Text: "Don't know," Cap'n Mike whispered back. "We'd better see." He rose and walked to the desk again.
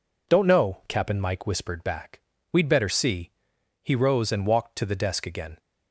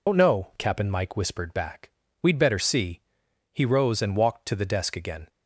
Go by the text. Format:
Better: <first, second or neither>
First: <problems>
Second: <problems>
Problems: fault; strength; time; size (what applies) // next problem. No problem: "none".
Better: first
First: none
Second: loses the start of "Don't"; at 0.0 s; 90 ms